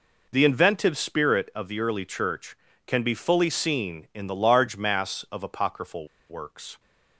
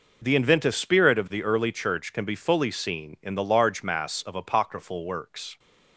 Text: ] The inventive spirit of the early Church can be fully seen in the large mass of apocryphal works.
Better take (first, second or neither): second